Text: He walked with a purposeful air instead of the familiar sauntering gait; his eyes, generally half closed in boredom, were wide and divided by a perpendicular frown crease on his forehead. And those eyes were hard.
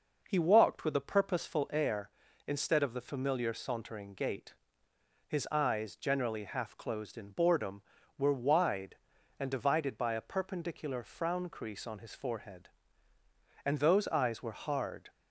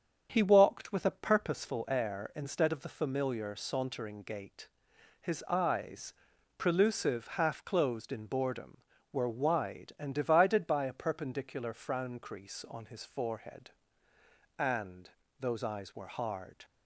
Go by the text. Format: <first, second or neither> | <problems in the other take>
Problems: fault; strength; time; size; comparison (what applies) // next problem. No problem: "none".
first | starts louder than the rest; until 1.3 s; 7 dB // says "prelusive" for "generally"; at 6.5 s // pauses between "And" and "those"; slight; at 15.1 s; 0.30 s long